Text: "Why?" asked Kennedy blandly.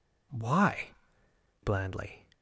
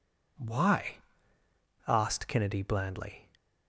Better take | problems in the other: second | skips "asked Kennedy"; at 1.2 s

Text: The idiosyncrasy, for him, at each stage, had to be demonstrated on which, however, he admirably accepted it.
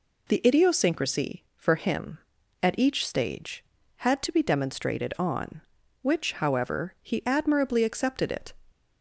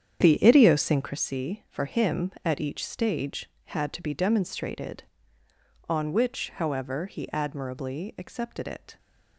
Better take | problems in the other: first | starts louder than the rest; strong; until 1.3 s; 8.5 dB

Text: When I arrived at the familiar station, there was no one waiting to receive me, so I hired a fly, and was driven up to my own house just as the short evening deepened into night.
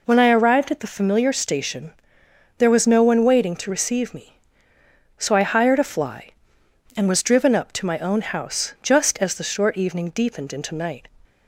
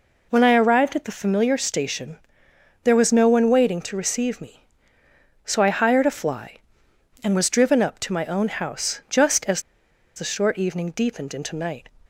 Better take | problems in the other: first | pauses between "as" and "the"; noticeable; at 9.6 s; 0.54 s long

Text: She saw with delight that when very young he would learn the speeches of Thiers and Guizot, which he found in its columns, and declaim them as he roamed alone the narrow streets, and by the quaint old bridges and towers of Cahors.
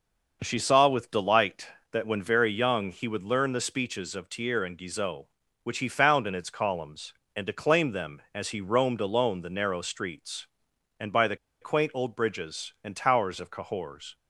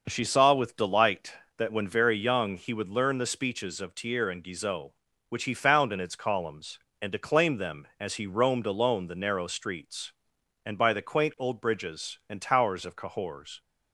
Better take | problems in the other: second | pauses between "the" and "quaint"; slight; at 11.3 s; 0.25 s long

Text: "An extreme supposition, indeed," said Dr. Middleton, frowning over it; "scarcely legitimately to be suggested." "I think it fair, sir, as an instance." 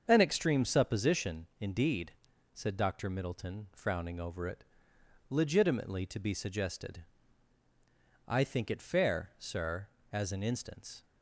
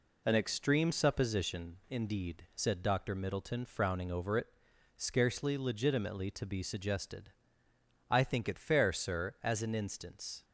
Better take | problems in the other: second | starts louder than the rest; until 1.0 s; 7 dB // skips "scarcely"; at 4.9 s

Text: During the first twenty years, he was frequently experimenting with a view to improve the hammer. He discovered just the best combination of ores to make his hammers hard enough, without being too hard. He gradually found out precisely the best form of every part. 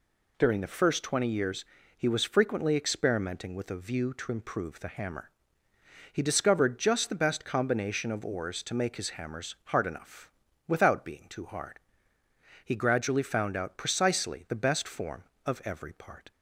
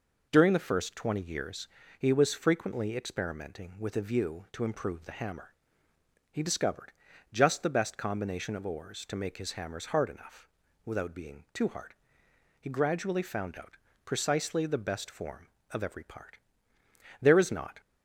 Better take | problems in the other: first | pauses between "discovered" and "just"; at 6.9 s; 0.40 s long // pauses between "out" and "precisely"; slight; at 13.7 s; 0.28 s long // goes on to say "There is not"; from 17.2 s on; 0.58 s long

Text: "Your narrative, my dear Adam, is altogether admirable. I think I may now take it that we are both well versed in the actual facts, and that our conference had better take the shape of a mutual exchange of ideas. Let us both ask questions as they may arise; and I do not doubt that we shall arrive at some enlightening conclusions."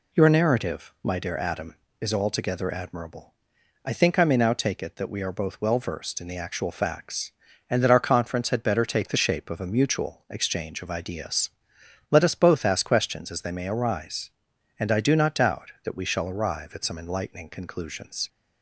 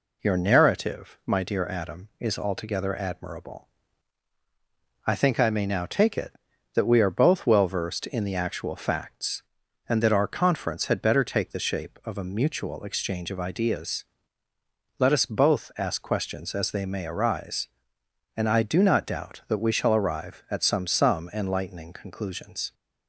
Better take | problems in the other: first | says "some" twice; at 20.8 s

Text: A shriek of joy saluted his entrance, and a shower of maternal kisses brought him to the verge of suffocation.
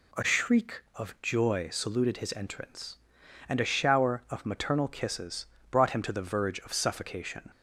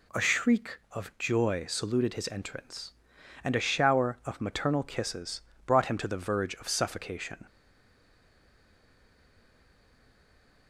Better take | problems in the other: first | pauses between "kisses" and "brought"; slight; at 5.4 s; 0.24 s long; slight in the first // stays silent after the last word; strong; from 7.4 s on; 3.2 s long

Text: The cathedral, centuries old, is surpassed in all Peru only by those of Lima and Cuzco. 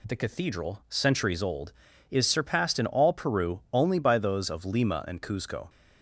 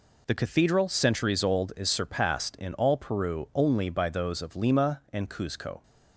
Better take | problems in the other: neither | none

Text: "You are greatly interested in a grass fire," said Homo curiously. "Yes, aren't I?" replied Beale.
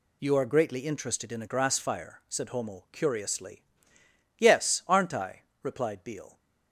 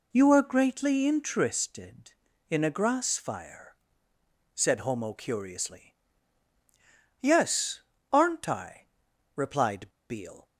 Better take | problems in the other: first | pauses between "replied" and "Beale"; slight; at 9.8 s; 0.21 s long

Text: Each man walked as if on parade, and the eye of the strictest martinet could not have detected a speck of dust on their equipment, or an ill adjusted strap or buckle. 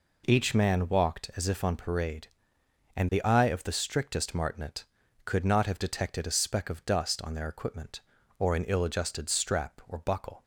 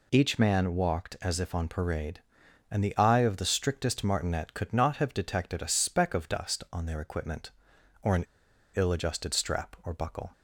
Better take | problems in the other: first | pauses between "an" and "ill"; noticeable; at 8.2 s; 0.49 s long

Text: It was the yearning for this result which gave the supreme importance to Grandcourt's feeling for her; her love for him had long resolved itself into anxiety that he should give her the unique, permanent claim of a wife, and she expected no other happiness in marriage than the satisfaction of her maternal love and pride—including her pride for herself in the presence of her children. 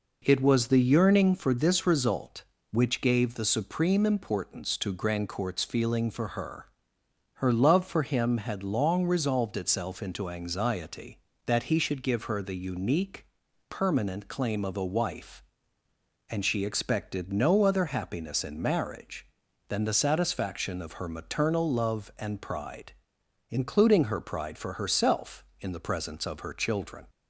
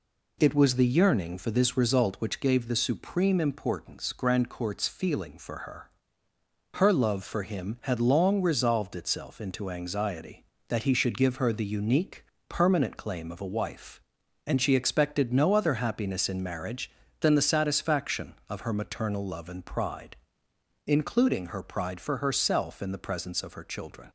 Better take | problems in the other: first | skips "to"; at 4.1 s

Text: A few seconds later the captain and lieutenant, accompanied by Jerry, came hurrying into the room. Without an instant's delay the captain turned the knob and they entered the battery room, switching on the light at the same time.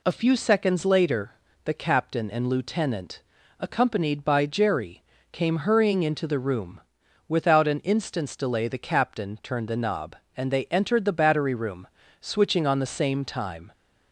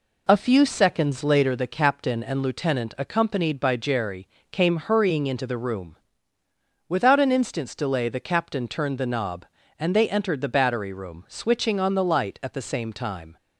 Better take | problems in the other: second | pauses between "later" and "the"; slight; at 1.3 s; 0.32 s long // skips "light at the"; at 12.9 s

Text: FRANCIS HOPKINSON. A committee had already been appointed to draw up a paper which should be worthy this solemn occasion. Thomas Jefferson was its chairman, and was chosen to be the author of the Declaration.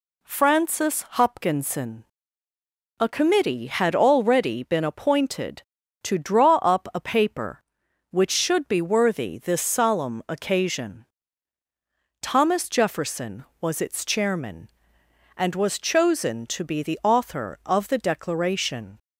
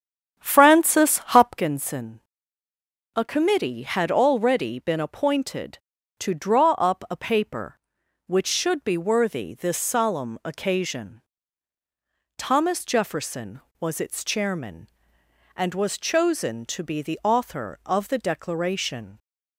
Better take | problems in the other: first | starts louder than the rest; strong; until 1.7 s; 9 dB

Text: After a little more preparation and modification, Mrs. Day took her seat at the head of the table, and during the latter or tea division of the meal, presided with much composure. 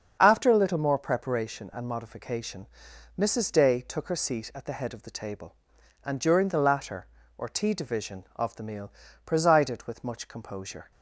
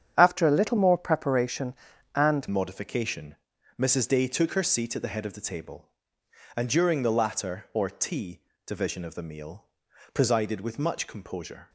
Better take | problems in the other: first | starts louder than the rest; strong; until 1.1 s; 8.5 dB; also in the first // changes voice at "modification"; from 2.5 s on; 9.1 s long // pauses between "tea" and "division"; slight; at 8.4 s; 0.22 s long

